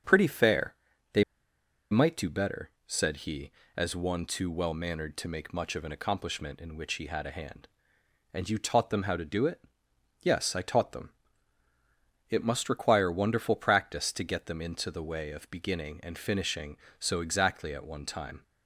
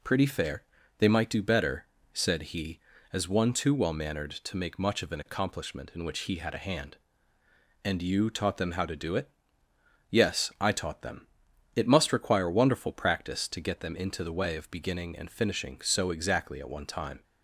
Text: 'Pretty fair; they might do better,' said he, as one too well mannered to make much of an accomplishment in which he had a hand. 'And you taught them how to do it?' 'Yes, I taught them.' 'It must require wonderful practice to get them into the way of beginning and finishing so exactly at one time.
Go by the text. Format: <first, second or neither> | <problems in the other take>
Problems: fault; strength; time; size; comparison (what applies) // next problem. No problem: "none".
second | starts louder than the rest; strong; until 2.1 s; 7 dB // pauses between "they" and "might"; noticeable; at 1.2 s; 0.68 s long